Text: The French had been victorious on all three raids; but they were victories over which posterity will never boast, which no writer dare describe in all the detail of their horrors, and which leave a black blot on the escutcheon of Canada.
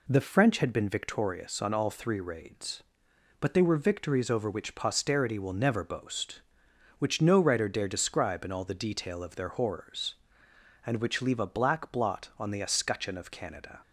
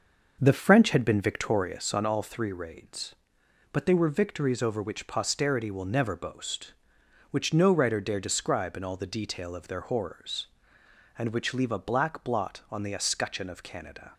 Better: first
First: none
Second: starts louder than the rest; noticeable; until 2.1 s; 6 dB

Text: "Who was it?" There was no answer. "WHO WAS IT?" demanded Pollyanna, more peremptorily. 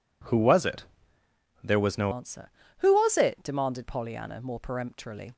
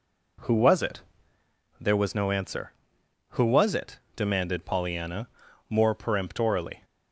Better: second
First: changes voice at "answer"; from 2.1 s on; 3.2 s long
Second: none

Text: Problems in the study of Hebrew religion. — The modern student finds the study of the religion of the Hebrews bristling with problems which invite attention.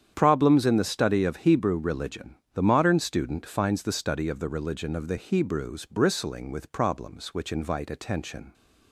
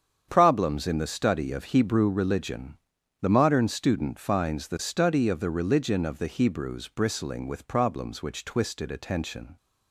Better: first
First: starts louder than the rest; strong; until 1.1 s; 8.5 dB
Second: starts louder than the rest; strong; until 1.3 s; 8 dB // says "twisted" for "invite"; at 8.4 s

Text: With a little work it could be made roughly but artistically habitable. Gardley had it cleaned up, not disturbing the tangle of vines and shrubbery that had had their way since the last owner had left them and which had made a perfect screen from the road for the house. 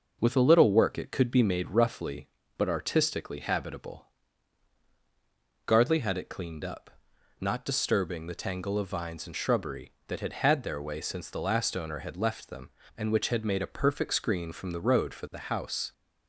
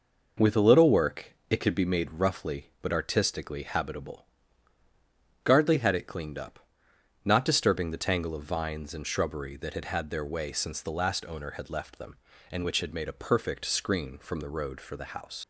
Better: first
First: none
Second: pauses between "work" and "it"; slight; at 1.3 s; 0.16 s long // leaves "house" unfinished; at 15.4 s; 50 ms

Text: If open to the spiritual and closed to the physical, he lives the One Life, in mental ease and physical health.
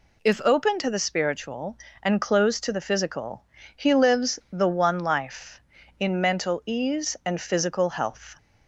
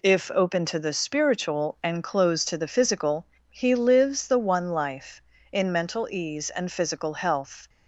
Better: neither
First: none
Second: none

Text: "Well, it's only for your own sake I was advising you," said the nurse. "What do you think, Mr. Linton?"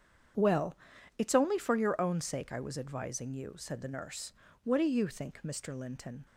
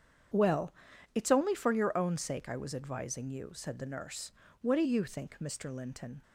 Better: neither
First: starts louder than the rest; strong; until 1.7 s; 8 dB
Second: starts louder than the rest; strong; until 1.7 s; 8.5 dB

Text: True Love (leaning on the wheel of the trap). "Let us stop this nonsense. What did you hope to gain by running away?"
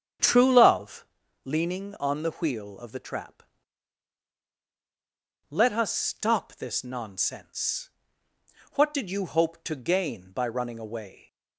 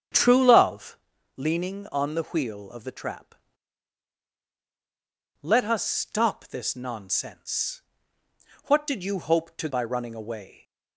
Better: first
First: starts louder than the rest; strong; until 1.5 s; 8.5 dB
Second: starts louder than the rest; strong; until 1.5 s; 8.5 dB // skips "gain"; at 9.6 s

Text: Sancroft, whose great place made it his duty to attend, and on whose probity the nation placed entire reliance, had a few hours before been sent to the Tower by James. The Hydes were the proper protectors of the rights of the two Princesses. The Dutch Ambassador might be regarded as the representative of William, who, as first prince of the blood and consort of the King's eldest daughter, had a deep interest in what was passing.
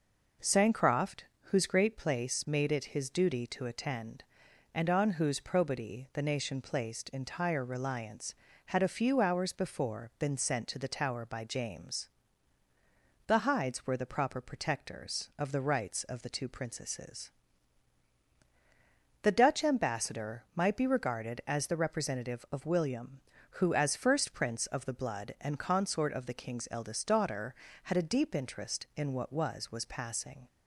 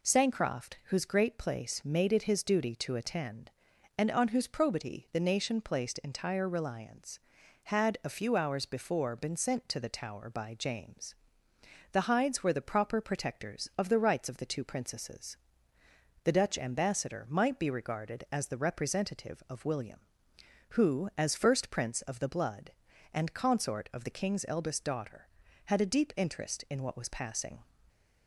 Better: second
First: says "was" twice; at 29.7 s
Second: none

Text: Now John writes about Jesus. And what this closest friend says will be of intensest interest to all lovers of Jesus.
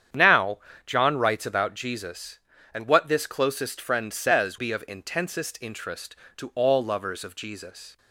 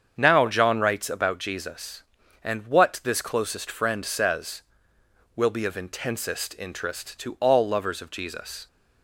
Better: second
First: starts louder than the rest; strong; until 1.4 s; 8.5 dB // pauses between "Now" and "John"; slight; at 0.5 s; 0.28 s long // skips "will"; at 4.5 s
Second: starts louder than the rest; strong; until 1.2 s; 7.5 dB

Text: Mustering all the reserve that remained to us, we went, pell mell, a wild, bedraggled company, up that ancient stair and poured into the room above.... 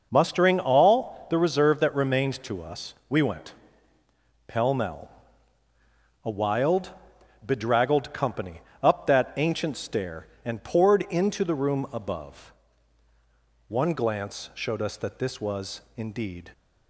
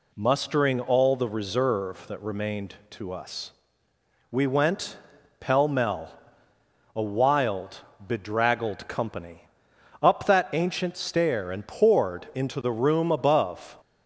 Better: second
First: goes on to say "One glance showed us that this was indeed"; strong; from 13.7 s on; 2.8 s long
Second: none

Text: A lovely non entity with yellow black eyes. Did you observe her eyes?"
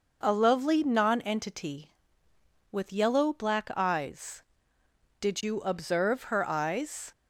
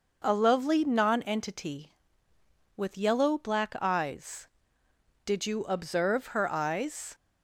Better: neither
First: none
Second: none

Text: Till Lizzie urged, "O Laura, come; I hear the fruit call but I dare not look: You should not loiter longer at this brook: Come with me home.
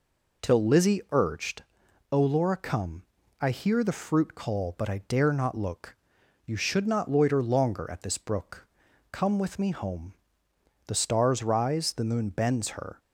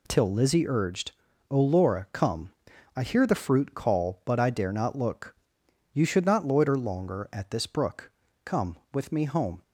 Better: second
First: goes on to say "The stars rise the moon bends her"; strong; from 10.8 s on; 2.1 s long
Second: none

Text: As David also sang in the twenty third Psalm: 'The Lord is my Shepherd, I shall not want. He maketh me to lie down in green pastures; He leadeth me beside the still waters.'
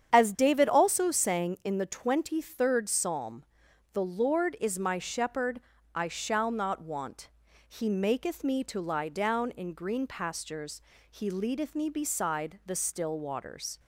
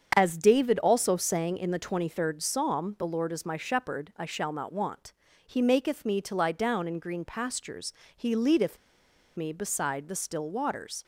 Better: first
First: starts louder than the rest; strong; until 1.1 s; 8.5 dB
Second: starts louder than the rest; strong; until 1.1 s; 7.5 dB // pauses between "leadeth" and "me"; noticeable; at 8.7 s; 0.58 s long

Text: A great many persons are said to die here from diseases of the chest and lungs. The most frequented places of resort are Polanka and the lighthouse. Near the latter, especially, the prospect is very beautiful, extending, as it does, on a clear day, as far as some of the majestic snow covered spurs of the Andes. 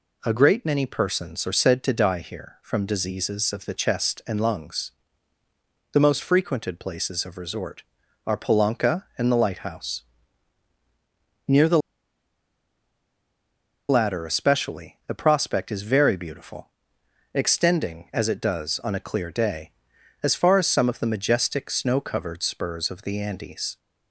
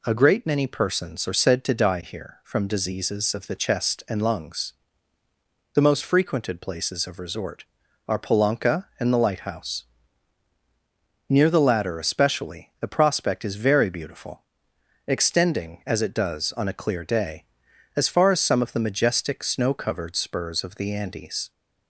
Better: second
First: pauses between "the" and "latter"; strong; at 11.7 s; 2.1 s long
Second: none

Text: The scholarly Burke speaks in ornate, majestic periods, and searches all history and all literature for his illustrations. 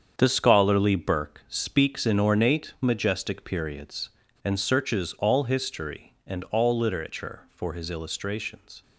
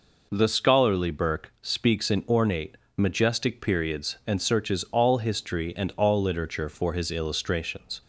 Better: second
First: gets quieter; strong; throughout; 9.5 dB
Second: none

